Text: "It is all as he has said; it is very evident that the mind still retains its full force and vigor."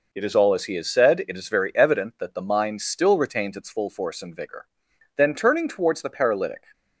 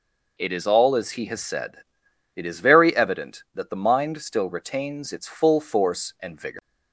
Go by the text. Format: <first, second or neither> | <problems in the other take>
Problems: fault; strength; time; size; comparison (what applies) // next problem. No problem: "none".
second | goes on to say "Then turning towards the paralytic"; from 5.1 s on; 1.4 s long